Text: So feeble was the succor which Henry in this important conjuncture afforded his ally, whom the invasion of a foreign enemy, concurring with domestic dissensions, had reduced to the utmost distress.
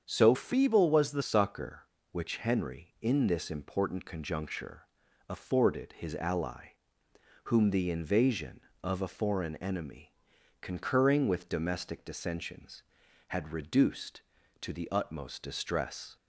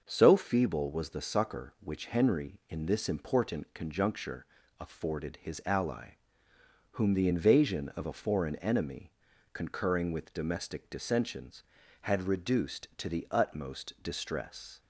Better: second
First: starts louder than the rest; strong; until 1.0 s; 7.5 dB // changes voice from "feeble" to "the"; from 0.3 to 1.2 s; 0.9 s long // pauses between "conjuncture" and "afforded"; at 4.8 s; 0.40 s long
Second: starts louder than the rest; until 1.0 s; 6.5 dB // pauses between "conjuncture" and "afforded"; slight; at 4.4 s; 0.32 s long

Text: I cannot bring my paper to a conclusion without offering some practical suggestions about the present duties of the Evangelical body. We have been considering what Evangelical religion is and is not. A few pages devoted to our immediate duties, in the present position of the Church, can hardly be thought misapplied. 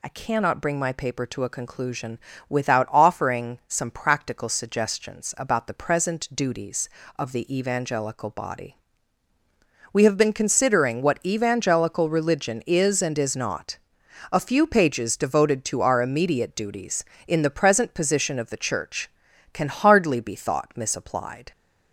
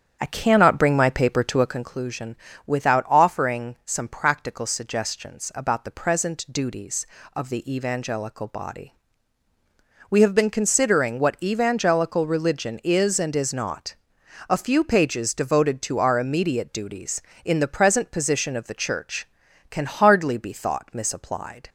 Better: first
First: pauses between "conclusion" and "without"; slight; at 2.1 s; 0.32 s long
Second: starts louder than the rest; strong; until 1.9 s; 8 dB // pauses between "conclusion" and "without"; slight; at 2.3 s; 0.32 s long

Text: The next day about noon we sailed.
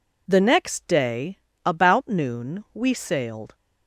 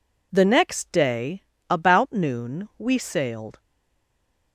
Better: first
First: pauses between "day" and "about"; slight; at 1.3 s; 0.26 s long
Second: pauses between "day" and "about"; slight; at 1.4 s; 0.26 s long // stays silent after the last word; from 3.5 s on; 1.0 s long

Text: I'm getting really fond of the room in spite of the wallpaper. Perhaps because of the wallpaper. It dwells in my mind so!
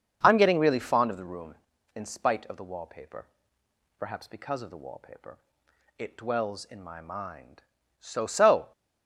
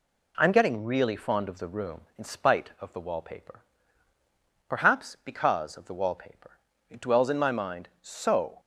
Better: second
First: starts louder than the rest; until 1.2 s; 7 dB // says "so" twice; at 8.2 s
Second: none

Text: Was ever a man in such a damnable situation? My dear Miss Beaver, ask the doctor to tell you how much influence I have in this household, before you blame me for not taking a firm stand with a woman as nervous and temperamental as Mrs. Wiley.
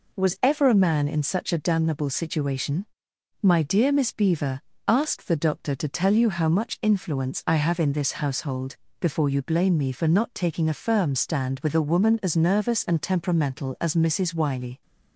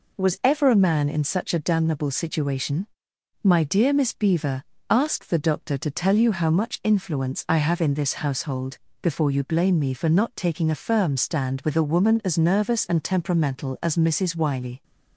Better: neither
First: none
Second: none

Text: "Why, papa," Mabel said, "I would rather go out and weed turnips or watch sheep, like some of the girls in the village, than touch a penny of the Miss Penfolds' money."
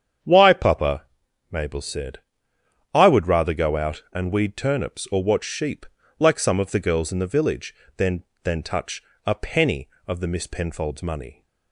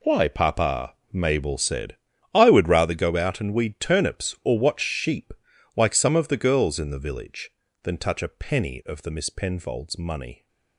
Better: second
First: starts louder than the rest; strong; until 1.6 s; 8 dB // says "than" twice; at 8.4 s // pauses between "touch" and "a"; slight; at 9.0 s; 0.22 s long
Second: none

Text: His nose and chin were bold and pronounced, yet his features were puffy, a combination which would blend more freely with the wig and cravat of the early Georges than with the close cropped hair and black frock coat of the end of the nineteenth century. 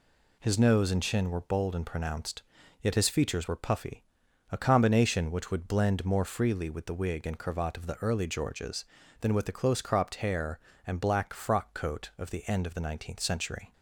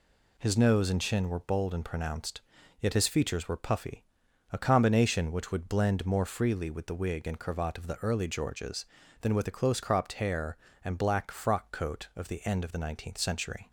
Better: neither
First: none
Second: none

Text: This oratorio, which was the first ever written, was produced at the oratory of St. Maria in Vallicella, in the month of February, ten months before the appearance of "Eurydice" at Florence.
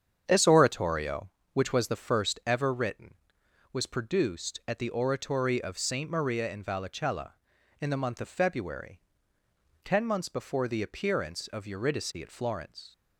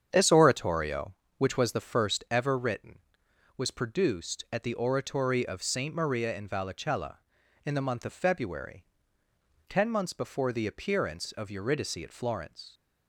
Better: neither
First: starts louder than the rest; strong; until 1.2 s; 8 dB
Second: starts louder than the rest; strong; until 1.1 s; 8 dB

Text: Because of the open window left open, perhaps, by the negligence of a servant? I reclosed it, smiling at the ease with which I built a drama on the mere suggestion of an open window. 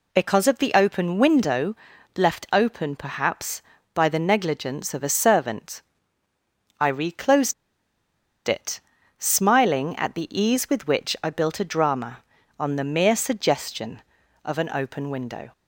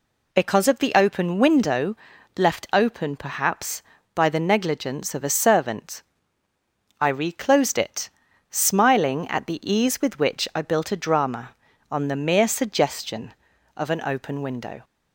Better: second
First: pauses between "window" and "left"; at 1.7 s; 0.40 s long // pauses between "reclosed" and "it"; noticeable; at 7.5 s; 0.94 s long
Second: pauses between "window" and "left"; at 1.9 s; 0.40 s long

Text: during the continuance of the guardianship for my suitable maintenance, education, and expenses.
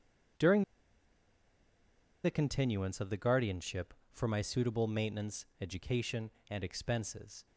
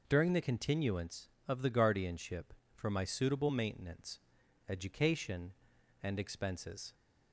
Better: second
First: pauses between "during" and "the"; strong; at 0.6 s; 1.6 s long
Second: none

